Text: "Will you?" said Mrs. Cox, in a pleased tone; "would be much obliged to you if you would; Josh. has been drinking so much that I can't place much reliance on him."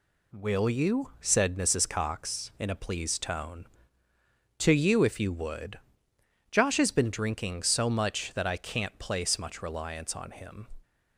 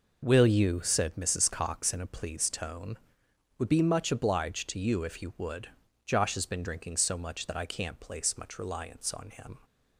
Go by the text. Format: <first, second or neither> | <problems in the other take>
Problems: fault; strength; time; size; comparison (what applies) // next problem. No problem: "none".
second | skips "would be much obliged"; at 4.1 s